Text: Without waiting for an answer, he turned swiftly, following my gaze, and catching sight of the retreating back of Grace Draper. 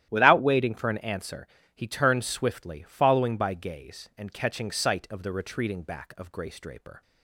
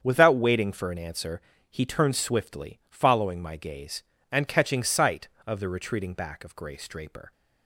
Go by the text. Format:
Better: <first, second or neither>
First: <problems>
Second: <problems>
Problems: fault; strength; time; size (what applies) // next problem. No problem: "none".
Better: second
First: starts louder than the rest; strong; until 1.1 s; 12 dB // says "by" for "my"; at 3.3 s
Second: starts louder than the rest; strong; until 1.0 s; 7.5 dB